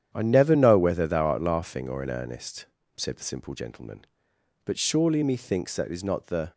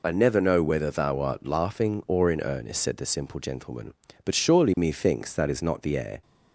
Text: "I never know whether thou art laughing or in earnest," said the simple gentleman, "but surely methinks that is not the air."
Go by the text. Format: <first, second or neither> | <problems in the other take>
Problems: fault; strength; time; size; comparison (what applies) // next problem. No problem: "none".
second | starts louder than the rest; strong; until 1.1 s; 9.5 dB // stops before "air"; at 6.5 s